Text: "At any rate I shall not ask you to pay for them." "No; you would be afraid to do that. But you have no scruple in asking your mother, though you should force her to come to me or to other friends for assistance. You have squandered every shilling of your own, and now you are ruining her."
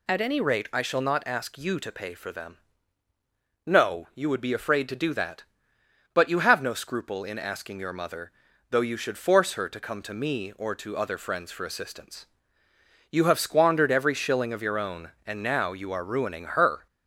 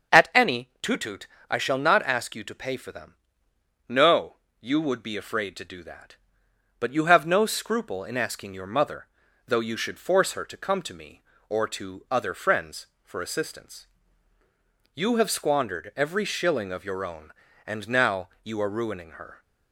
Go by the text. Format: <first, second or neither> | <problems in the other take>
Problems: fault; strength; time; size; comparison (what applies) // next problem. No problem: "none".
first | starts louder than the rest; until 1.5 s; 7 dB // says "tutut" for "rate"; at 0.8 s